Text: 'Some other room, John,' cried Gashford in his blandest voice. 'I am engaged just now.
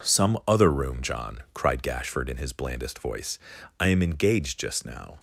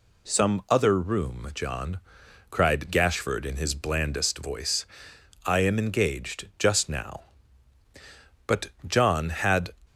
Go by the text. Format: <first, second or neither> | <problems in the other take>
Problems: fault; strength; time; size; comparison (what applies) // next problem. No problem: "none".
first | goes on to say "But John had"; noticeable; from 8.4 s on; 1.2 s long